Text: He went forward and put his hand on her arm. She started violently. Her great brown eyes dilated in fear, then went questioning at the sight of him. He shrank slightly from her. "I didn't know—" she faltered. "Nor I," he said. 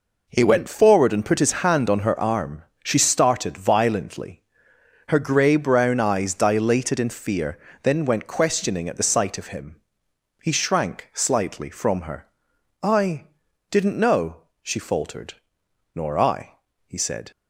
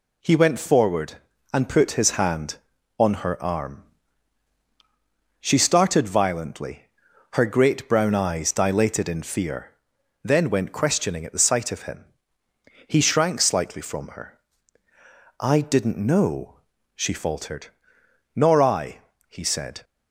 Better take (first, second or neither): second